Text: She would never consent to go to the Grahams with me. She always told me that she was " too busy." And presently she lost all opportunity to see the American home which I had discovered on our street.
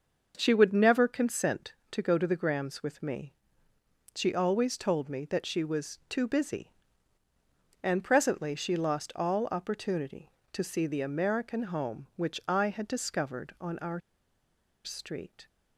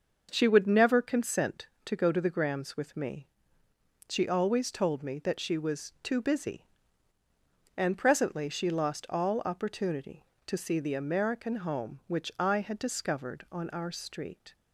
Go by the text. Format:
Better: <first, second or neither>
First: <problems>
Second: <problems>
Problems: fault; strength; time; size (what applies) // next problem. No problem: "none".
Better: second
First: starts louder than the rest; until 1.3 s; 6.5 dB // pauses between "our" and "street"; noticeable; at 14.0 s; 0.85 s long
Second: starts louder than the rest; until 1.3 s; 6.5 dB